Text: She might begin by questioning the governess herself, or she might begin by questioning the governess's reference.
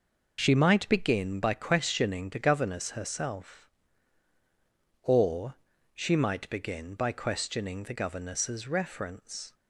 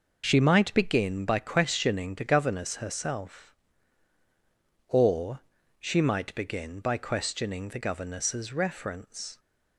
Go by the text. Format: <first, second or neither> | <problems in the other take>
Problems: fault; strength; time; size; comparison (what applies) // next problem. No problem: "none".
neither | pauses between "or" and "she"; the same in both